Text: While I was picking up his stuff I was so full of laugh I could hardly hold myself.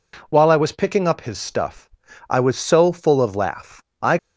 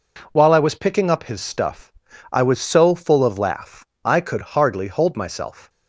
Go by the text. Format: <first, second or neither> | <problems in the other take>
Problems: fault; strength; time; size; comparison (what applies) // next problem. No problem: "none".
second | pauses between "stuff" and "I"; at 1.9 s; 0.40 s long; also in the second // pauses between "laugh" and "I"; slight; at 3.8 s; 0.18 s long; slight in the second // stops before "could hardly hold myself"; at 4.1 s